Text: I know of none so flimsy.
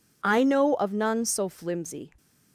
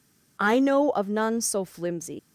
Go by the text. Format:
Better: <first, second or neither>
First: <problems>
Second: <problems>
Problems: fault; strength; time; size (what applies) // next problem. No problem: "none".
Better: first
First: none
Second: leaves "flimsy" unfinished; at 2.1 s; 130 ms